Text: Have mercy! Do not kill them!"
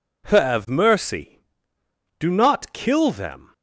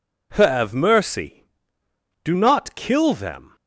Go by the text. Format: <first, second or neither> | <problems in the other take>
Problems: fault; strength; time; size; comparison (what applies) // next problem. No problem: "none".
neither | none